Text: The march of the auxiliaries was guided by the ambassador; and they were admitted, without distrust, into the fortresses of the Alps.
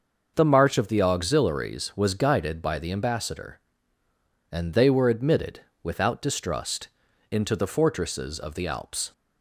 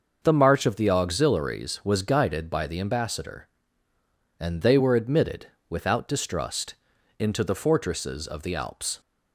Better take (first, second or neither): neither